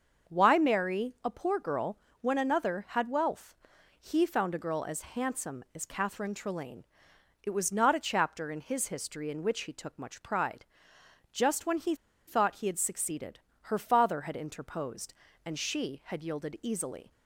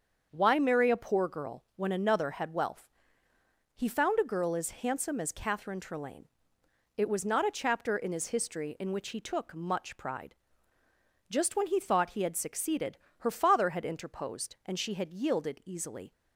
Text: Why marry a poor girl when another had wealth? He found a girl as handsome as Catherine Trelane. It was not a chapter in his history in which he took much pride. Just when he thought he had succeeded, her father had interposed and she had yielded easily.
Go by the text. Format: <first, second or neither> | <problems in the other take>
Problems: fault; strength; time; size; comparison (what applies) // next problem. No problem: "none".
second | starts louder than the rest; until 1.3 s; 6.5 dB; also in the second // pauses between "girl" and "when"; slight; at 1.9 s; 0.22 s long // pauses between "he" and "thought"; slight; at 11.9 s; 0.32 s long